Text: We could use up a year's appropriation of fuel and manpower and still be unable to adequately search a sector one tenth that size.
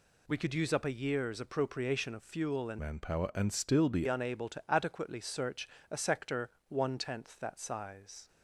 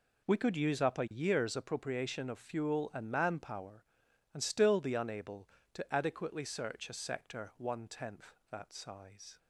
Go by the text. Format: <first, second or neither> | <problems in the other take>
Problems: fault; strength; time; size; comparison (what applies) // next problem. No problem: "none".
second | changes voice from "manpower" to "be"; from 2.7 to 4.0 s; 1.3 s long // pauses between "search" and "a"; slight; at 5.6 s; 0.22 s long // pauses between "sector" and "one"; slight; at 6.4 s; 0.20 s long